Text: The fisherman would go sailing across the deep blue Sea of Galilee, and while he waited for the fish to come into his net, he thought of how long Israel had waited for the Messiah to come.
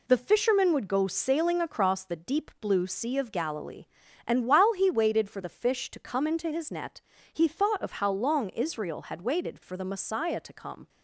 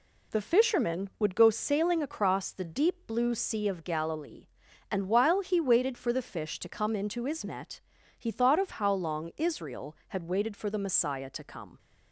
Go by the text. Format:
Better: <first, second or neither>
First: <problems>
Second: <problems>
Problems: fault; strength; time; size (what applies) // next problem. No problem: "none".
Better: neither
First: none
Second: none